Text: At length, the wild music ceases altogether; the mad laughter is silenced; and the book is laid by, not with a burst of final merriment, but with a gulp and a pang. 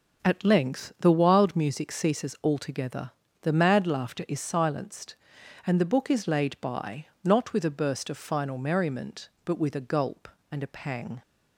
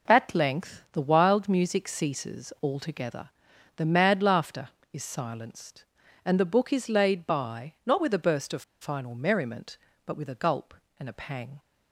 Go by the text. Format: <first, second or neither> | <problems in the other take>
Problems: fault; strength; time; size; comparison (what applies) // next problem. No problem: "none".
first | pauses between "of" and "final"; slight; at 8.6 s; 0.18 s long